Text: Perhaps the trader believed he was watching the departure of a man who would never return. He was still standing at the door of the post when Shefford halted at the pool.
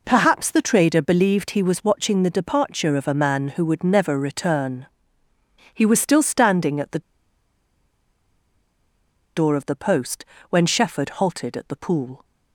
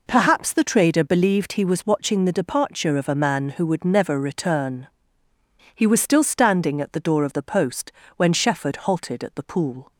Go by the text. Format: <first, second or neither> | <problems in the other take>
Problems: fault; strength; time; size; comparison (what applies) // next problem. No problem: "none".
second | pauses between "the" and "door"; strong; at 6.9 s; 2.3 s long // pauses between "post" and "when"; slight; at 10.2 s; 0.26 s long; slight in the second